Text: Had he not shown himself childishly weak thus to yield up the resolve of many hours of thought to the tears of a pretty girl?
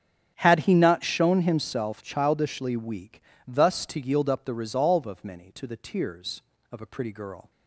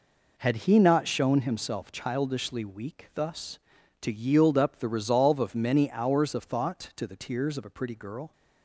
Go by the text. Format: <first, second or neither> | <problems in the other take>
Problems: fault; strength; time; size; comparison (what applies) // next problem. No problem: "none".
second | starts louder than the rest; strong; until 1.3 s; 8.5 dB // pauses between "weak" and "thus"; slight; at 3.1 s; 0.26 s long // skips "hours of thought"; at 5.5 s